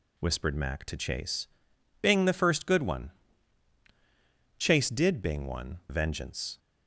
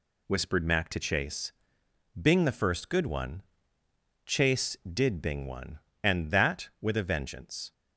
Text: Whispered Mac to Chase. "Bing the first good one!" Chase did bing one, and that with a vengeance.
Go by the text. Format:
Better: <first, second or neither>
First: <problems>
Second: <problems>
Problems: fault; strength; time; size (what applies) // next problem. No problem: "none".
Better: second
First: skips "and that with a"; at 5.8 s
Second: none